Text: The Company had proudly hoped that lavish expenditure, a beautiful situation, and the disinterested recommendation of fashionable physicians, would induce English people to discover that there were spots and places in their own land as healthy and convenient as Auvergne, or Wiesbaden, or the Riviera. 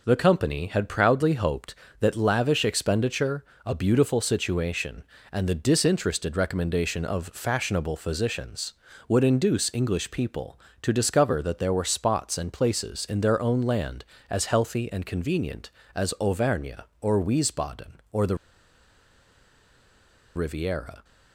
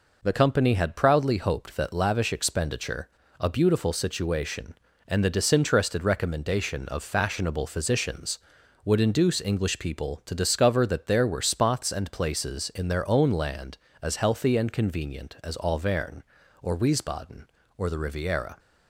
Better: second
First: pauses between "the" and "Riviera"; strong; at 18.3 s; 1.9 s long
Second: none

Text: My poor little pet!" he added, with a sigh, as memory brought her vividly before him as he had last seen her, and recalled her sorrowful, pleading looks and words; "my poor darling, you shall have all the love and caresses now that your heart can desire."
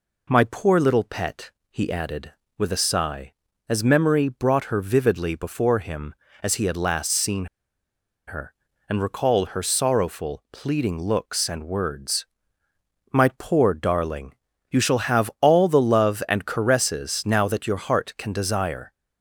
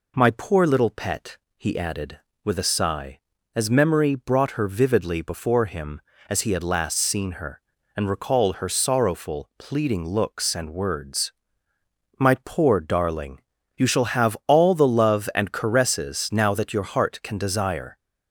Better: second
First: pauses between "seen" and "her"; noticeable; at 7.4 s; 0.80 s long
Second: none

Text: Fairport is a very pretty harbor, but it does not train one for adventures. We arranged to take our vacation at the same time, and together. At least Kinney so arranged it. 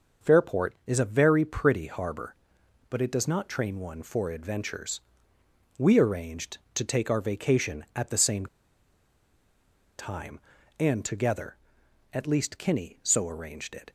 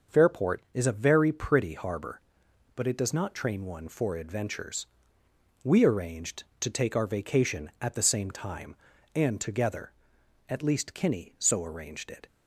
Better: second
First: starts louder than the rest; until 1.3 s; 6 dB // pauses between "same" and "time"; strong; at 8.4 s; 1.5 s long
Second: starts louder than the rest; until 1.2 s; 6 dB

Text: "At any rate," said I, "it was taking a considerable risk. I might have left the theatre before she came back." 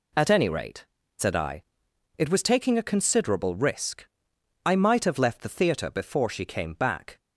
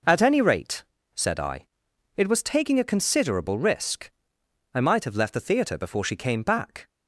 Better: neither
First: none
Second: none

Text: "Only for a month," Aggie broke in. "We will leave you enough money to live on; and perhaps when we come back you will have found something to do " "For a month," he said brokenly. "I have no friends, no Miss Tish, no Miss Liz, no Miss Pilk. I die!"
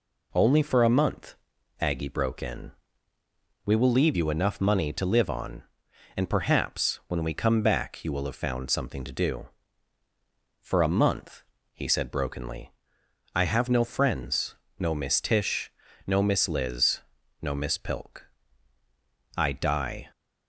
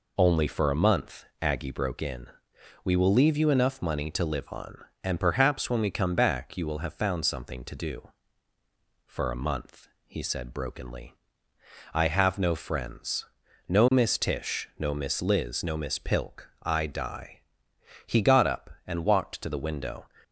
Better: first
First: none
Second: goes on to say "He got up and walked to the window"; strong; from 18.0 s on; 2.0 s long

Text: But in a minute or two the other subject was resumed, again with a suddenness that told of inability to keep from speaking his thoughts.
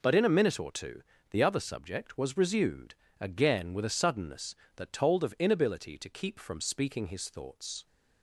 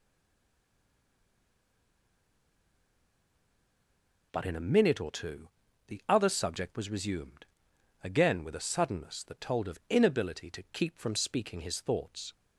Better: first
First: pauses between "two" and "the"; slight; at 1.0 s; 0.26 s long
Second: stays silent before the first word; strong; until 4.3 s; 4.3 s long // pauses between "two" and "the"; at 5.4 s; 0.40 s long

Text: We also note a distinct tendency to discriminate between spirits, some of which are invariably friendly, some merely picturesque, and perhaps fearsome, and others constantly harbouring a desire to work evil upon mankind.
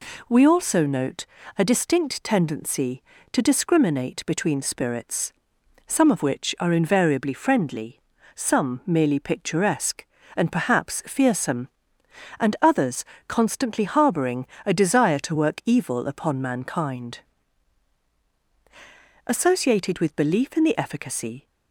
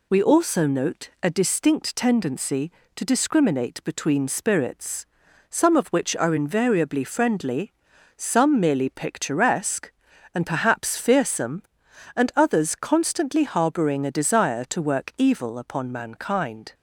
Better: second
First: pauses between "note" and "a"; slight; at 1.2 s; 0.30 s long // pauses between "others" and "constantly"; slight; at 13.0 s; 0.24 s long // pauses between "harbouring" and "a"; slight; at 14.4 s; 0.20 s long // goes on to say "Associated with belief in the efficacy"; strong; from 19.2 s on; 2.2 s long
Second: none

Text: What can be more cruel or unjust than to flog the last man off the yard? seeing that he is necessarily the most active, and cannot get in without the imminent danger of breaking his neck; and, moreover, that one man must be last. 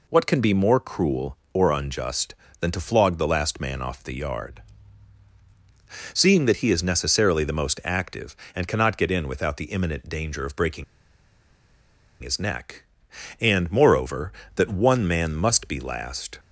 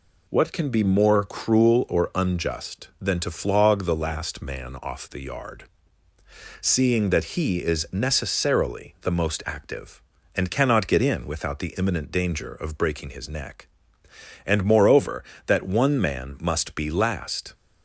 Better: second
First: pauses between "breaking" and "his"; strong; at 10.8 s; 1.3 s long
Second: none

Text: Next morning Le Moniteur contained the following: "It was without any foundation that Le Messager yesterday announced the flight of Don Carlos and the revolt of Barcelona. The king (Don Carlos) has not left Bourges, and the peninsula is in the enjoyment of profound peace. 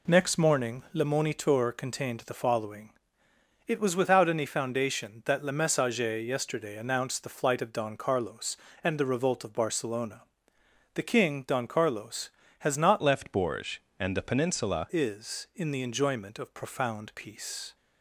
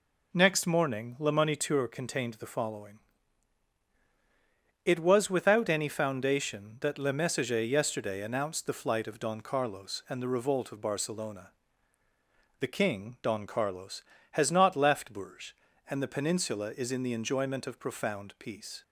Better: second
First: changes voice from "left" to "peninsula"; from 13.0 to 14.8 s; 1.8 s long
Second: none

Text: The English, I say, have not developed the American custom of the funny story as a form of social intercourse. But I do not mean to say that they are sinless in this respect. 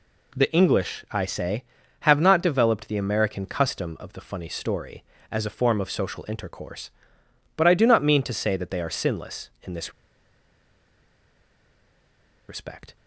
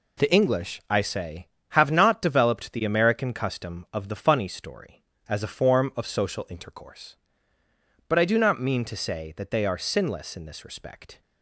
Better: second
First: pauses between "this" and "respect"; strong; at 9.9 s; 2.5 s long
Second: none

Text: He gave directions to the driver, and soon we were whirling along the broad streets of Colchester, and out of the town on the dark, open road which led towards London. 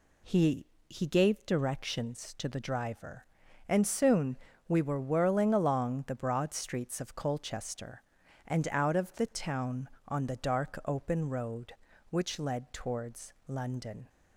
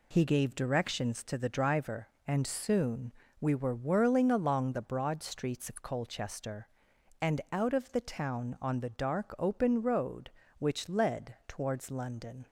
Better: second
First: says "He" twice; at 0.8 s // pauses between "soon" and "we"; slight; at 4.3 s; 0.28 s long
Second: pauses between "soon" and "we"; slight; at 3.1 s; 0.28 s long

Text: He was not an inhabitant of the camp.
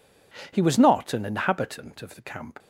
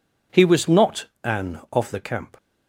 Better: first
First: none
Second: pauses between "not" and "an"; slight; at 1.0 s; 0.18 s long // skips "inhabitant"; at 1.6 s

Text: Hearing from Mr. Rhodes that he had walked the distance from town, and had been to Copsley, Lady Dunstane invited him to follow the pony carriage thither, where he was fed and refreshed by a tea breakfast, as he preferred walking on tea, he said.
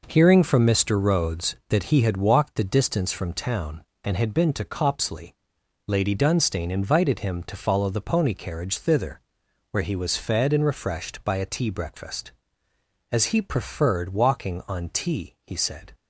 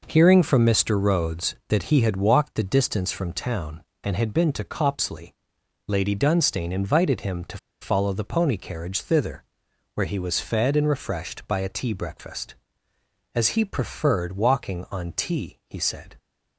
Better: first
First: none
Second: pauses between "to" and "follow"; slight; at 7.5 s; 0.23 s long

